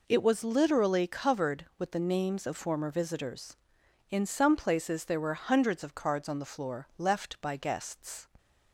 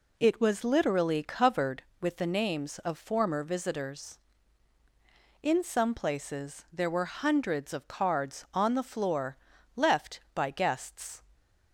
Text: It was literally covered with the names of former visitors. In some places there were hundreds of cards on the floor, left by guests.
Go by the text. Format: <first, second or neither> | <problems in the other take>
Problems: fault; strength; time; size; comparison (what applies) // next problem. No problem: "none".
neither | none